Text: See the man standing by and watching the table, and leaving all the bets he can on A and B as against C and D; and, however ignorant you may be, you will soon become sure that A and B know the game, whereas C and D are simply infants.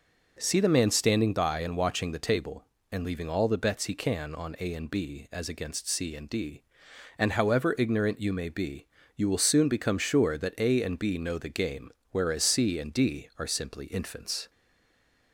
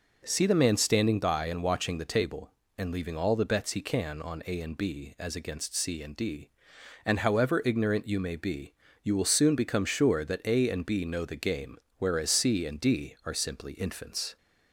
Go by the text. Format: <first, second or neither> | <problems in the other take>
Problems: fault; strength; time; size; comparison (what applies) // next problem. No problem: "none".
second | stays silent after the last word; slight; from 14.4 s on; 0.9 s long